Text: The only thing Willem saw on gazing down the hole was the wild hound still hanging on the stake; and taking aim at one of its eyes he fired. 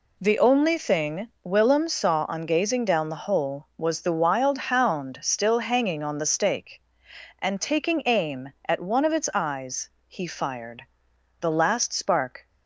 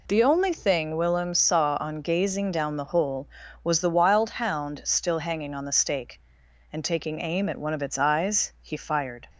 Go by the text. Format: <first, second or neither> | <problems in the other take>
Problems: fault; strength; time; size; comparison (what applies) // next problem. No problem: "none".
second | pauses between "eyes" and "he"; slight; at 9.8 s; 0.18 s long // goes on to say "The last spark"; noticeable; from 11.3 s on; 1.0 s long